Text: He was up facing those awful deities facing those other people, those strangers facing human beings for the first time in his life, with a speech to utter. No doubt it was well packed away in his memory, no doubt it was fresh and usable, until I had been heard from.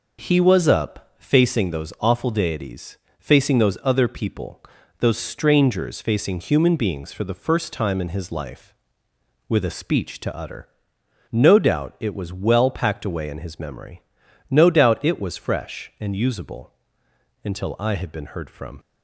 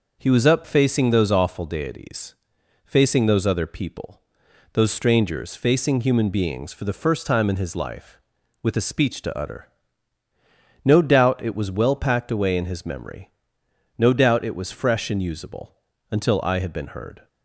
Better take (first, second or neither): first